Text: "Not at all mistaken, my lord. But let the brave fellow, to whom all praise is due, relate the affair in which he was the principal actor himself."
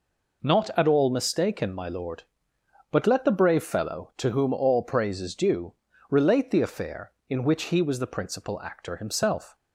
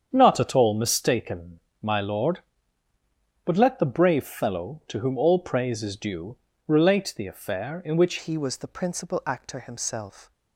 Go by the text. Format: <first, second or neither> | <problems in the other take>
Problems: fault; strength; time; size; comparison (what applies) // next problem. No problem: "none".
first | starts louder than the rest; strong; until 1.1 s; 8 dB // changes voice at "he"; from 8.1 s on; 2.2 s long